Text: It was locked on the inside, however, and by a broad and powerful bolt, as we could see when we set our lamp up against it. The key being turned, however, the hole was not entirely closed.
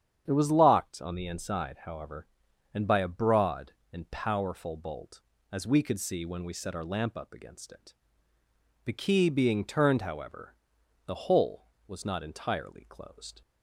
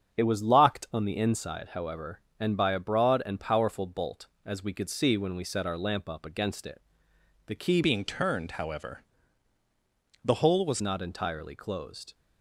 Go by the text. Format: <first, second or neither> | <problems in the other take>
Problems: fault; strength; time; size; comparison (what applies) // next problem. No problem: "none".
first | starts louder than the rest; strong; until 1.2 s; 7 dB; strong in the first // changes voice from "being" to "was"; from 7.8 to 10.8 s; 3.0 s long